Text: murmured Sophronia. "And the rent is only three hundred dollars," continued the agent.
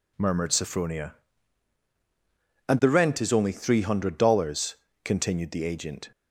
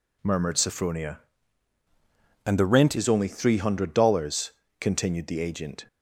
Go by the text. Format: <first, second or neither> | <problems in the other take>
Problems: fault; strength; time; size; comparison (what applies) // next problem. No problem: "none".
first | changes voice from "And" to "rent"; from 2.4 to 2.9 s; 0.5 s long